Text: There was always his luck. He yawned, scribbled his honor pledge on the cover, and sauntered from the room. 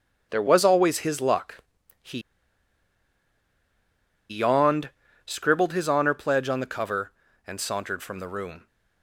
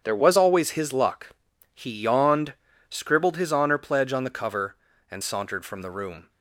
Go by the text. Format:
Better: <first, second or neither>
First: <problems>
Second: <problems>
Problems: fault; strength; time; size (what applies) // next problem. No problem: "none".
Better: second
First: starts louder than the rest; strong; until 1.3 s; 7.5 dB // pauses between "He" and "yawned"; strong; at 2.1 s; 2.1 s long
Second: starts louder than the rest; strong; until 1.0 s; 8 dB